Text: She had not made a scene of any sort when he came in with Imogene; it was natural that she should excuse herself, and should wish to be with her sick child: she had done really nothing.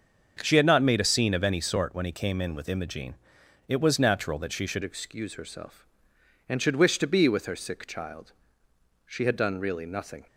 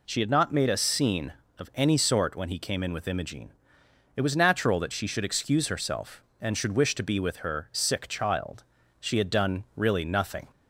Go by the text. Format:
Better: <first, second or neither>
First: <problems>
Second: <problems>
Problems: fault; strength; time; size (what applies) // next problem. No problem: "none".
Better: second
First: starts louder than the rest; until 1.4 s; 6.5 dB // changes voice at "excuse"; from 4.8 s on; 5.4 s long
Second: none